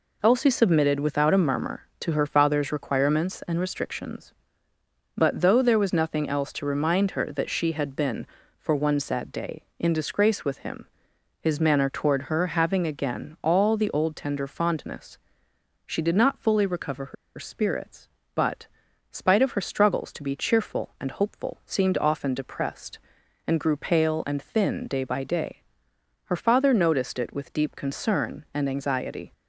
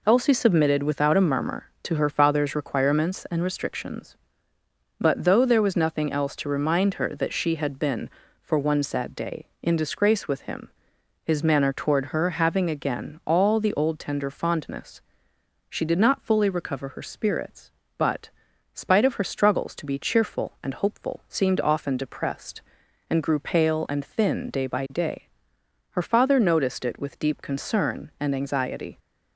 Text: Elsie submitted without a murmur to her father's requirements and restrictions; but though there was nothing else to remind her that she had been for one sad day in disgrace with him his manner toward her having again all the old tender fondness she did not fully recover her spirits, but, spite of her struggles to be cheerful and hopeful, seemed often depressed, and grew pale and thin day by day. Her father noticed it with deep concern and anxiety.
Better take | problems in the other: second | pauses between "him" and "his"; noticeable; at 10.8 s; 0.54 s long; noticeable in the second // pauses between "fondness" and "she"; noticeable; at 15.1 s; 0.68 s long; noticeable in the second // pauses between "her" and "spirits"; slight; at 17.1 s; 0.23 s long

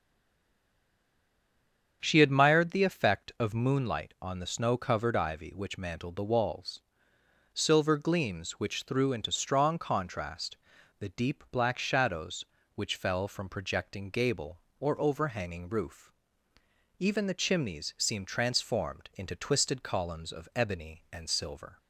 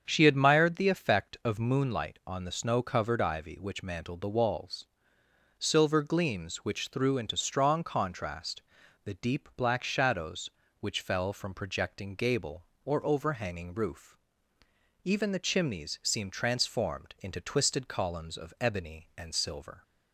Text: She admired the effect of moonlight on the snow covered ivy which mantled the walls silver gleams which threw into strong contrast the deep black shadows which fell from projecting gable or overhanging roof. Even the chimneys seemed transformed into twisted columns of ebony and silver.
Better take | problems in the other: second | stays silent before the first word; noticeable; until 2.0 s; 2.0 s long // starts louder than the rest; strong; until 3.0 s; 7.5 dB; strong in the second // pauses between "walls" and "silver"; noticeable; at 6.8 s; 0.72 s long; noticeable in the second // pauses between "contrast" and "the"; at 10.5 s; 0.40 s long; also in the second

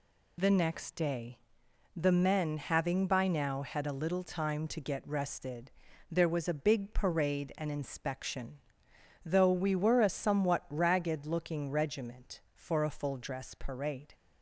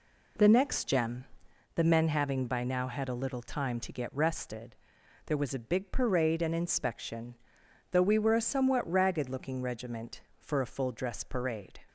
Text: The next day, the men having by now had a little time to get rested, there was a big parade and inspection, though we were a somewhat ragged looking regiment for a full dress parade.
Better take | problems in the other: first | says "gem" for "day"; at 0.8 s

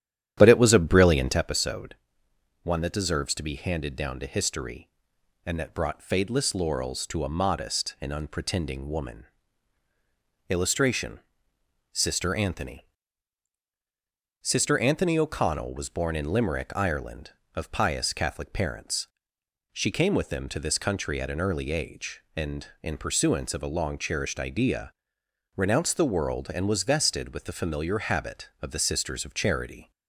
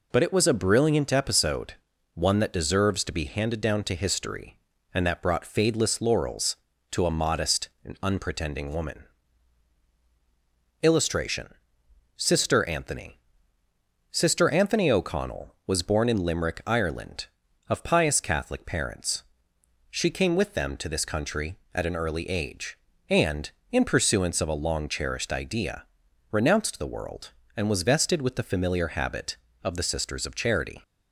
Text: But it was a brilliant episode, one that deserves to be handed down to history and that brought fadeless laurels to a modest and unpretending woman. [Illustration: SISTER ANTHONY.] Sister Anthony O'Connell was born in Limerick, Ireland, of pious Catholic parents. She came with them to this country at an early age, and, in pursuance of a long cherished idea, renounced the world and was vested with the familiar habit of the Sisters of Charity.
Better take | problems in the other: second | starts louder than the rest; strong; until 1.5 s; 10.5 dB

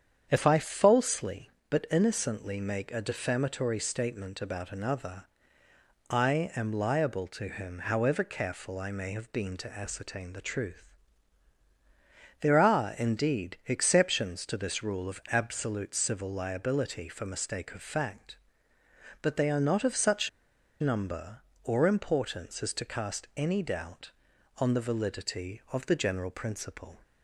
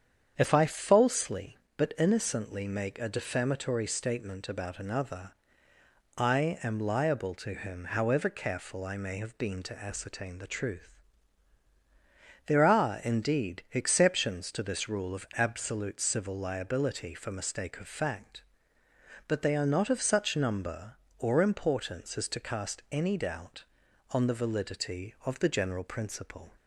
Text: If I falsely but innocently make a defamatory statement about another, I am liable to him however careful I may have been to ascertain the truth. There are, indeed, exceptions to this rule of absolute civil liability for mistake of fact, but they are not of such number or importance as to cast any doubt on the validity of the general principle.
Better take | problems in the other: second | starts louder than the rest; strong; until 1.3 s; 8 dB; strong in the second // pauses between "such" and "number"; noticeable; at 20.2 s; 0.51 s long

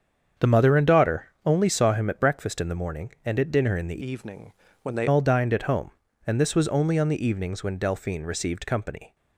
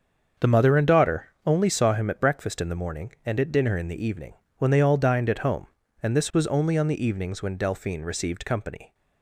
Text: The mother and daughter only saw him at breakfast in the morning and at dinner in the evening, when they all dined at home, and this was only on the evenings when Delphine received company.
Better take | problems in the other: second | starts louder than the rest; strong; until 1.5 s; 7.5 dB; also in the second // pauses between "daughter" and "only"; slight; at 1.2 s; 0.18 s long; slight in the second // changes voice from "evening" to "they"; from 4.0 to 5.0 s; 1.0 s long

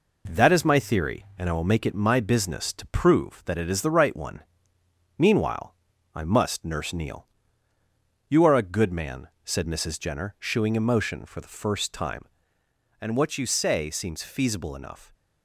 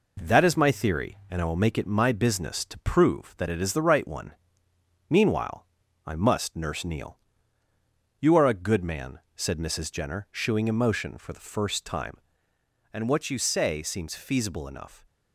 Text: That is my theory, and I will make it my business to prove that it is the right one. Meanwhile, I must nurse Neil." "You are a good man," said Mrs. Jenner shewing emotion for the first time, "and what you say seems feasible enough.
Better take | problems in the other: neither | none

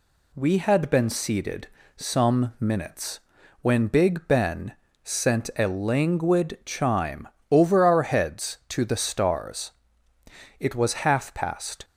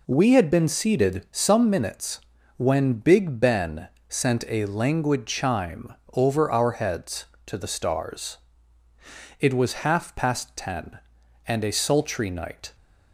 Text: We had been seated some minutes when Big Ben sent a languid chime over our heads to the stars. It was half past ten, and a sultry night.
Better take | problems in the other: second | pauses between "seated" and "some"; slight; at 1.6 s; 0.28 s long // pauses between "minutes" and "when"; at 3.2 s; 0.40 s long; slight in the second // pauses between "Ben" and "sent"; slight; at 4.7 s; 0.32 s long; slight in the second // pauses between "chime" and "over"; slight; at 7.2 s; 0.22 s long; slight in the second // stops before "ten and a sultry night"; at 11.8 s

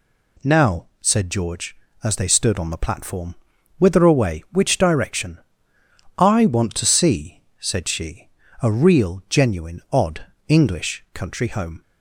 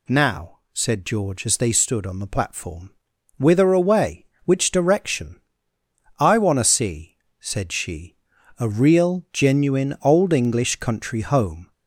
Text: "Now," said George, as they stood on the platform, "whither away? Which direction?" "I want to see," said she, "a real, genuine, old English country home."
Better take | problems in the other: second | says "odd" for "old"; at 9.9 s

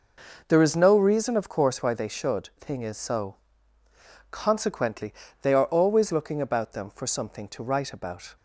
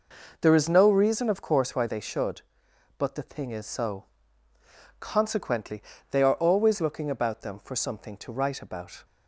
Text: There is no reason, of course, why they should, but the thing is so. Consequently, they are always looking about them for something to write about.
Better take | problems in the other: second | skips "but the"; at 2.5 s

